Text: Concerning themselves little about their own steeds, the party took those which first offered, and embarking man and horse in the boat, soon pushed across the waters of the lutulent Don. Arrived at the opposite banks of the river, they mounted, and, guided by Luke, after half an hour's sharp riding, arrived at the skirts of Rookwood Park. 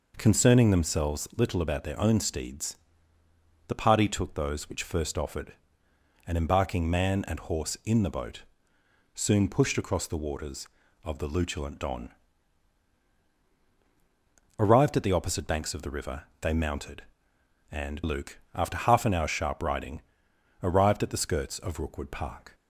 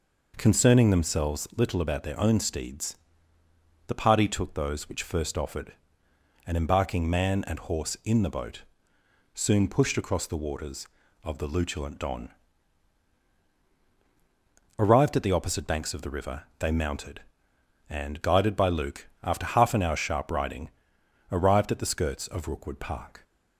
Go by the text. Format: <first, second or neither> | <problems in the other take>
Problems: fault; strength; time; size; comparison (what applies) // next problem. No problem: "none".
second | skips "guided by"; at 18.0 s